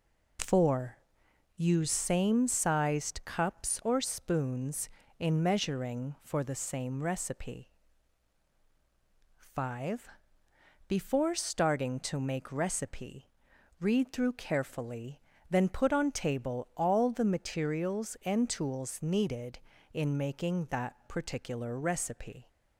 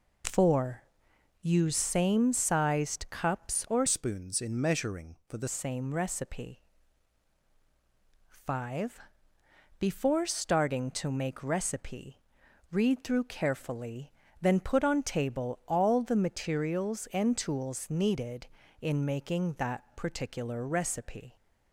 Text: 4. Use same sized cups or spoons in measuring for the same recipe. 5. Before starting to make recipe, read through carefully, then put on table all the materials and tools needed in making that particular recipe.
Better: first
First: none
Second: changes voice from "spoons" to "the"; from 3.8 to 5.4 s; 1.6 s long

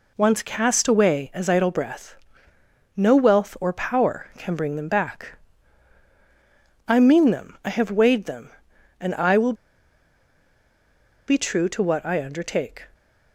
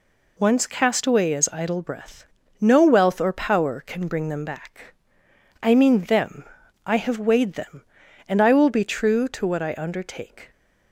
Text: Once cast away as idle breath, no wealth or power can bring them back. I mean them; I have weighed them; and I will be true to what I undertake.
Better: second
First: pauses between "will" and "be"; strong; at 9.5 s; 1.7 s long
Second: none

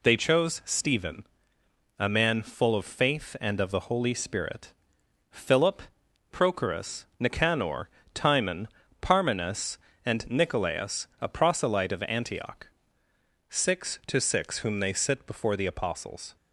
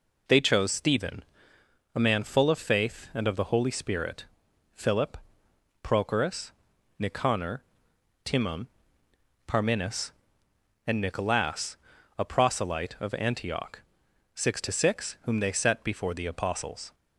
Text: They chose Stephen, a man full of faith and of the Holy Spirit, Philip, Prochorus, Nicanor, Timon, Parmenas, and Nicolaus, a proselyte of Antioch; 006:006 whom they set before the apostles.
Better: second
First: says "sit" for "set"; at 14.9 s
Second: none

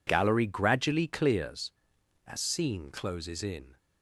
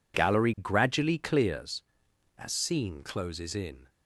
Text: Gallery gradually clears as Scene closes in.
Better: neither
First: none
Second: none

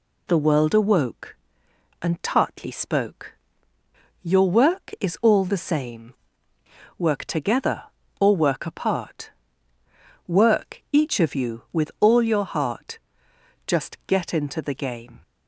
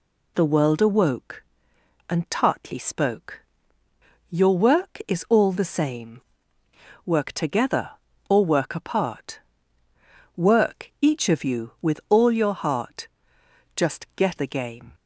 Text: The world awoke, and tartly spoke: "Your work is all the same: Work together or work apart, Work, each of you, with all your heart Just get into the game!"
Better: first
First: pauses between "heart" and "Just"; noticeable; at 12.9 s; 0.66 s long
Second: pauses between "heart" and "Just"; noticeable; at 13.0 s; 0.66 s long // skips "into"; at 14.3 s

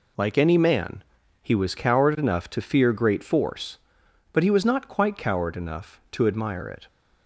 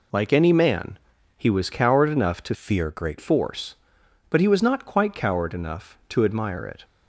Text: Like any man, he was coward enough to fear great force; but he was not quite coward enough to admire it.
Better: first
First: none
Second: changes voice from "fear" to "great"; from 2.5 to 3.1 s; 0.6 s long

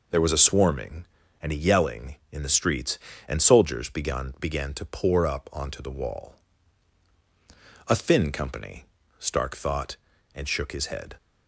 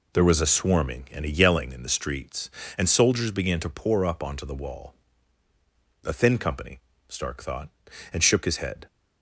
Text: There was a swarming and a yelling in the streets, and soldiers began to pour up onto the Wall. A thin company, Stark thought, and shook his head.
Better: second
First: says "began" twice; at 4.3 s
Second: none

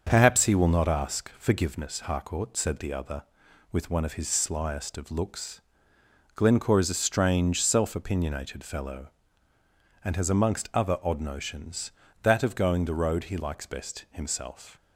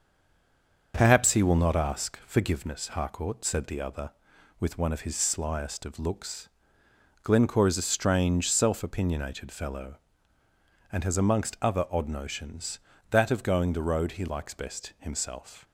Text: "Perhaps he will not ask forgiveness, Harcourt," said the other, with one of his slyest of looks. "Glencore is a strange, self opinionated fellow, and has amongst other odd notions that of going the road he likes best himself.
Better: first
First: starts louder than the rest; until 1.1 s; 6.5 dB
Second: stays silent before the first word; slight; until 0.9 s; 0.9 s long // starts louder than the rest; until 1.9 s; 6.5 dB

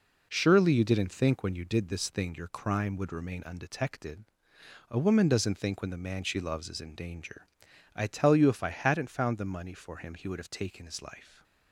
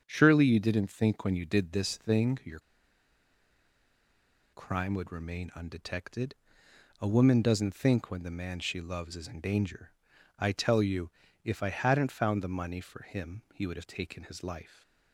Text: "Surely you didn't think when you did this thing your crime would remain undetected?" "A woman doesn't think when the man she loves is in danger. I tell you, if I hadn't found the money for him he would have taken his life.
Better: first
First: none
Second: starts louder than the rest; strong; until 1.0 s; 7 dB // pauses between "your" and "crime"; strong; at 2.5 s; 1.9 s long

